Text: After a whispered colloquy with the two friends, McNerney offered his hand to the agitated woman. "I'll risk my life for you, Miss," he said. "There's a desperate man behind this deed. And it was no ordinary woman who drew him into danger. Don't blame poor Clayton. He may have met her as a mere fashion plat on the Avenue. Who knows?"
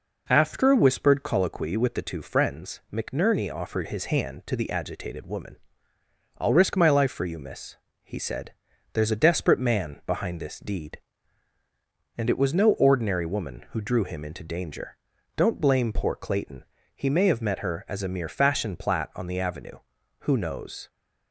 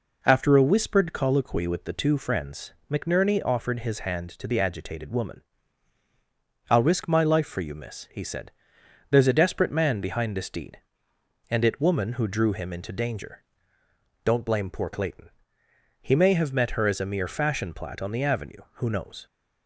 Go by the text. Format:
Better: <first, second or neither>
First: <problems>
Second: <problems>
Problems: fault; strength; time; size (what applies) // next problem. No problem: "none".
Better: first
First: none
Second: skips "was no ordinary"; at 11.8 s